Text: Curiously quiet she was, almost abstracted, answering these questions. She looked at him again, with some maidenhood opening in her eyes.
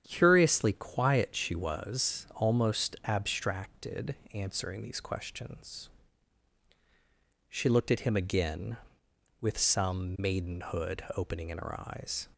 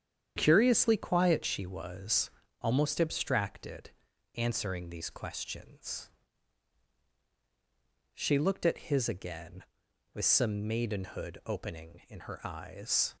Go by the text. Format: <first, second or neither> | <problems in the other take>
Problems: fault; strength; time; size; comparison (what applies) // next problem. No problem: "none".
first | starts louder than the rest; strong; until 1.3 s; 8.5 dB; strong in the first // says "his" for "him"; at 8.8 s